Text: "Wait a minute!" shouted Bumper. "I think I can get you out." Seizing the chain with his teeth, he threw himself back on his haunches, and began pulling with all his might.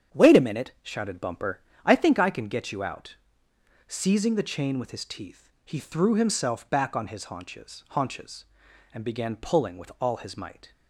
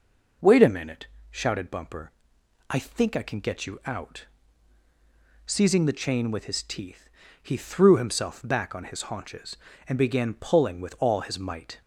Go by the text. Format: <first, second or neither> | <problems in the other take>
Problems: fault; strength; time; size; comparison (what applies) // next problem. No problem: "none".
second | starts louder than the rest; strong; until 1.2 s; 8.5 dB // says "haunches" twice; at 7.9 s